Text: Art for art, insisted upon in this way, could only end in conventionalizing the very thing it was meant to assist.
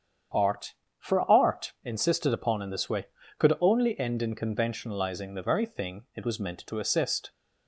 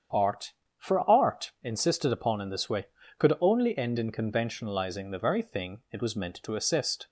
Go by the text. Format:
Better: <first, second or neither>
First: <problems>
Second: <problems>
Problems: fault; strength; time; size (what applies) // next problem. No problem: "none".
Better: neither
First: starts louder than the rest; strong; until 1.6 s; 8 dB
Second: starts louder than the rest; strong; until 1.4 s; 8 dB